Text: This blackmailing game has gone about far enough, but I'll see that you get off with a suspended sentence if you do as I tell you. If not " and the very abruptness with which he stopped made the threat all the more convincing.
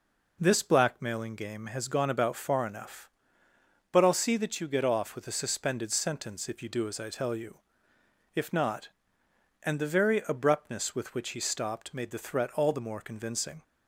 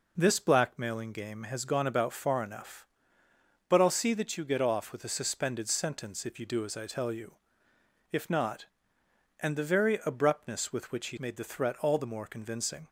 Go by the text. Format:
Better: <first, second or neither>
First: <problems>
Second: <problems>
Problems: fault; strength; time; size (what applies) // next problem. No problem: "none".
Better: first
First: none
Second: skips "stopped"; at 11.1 s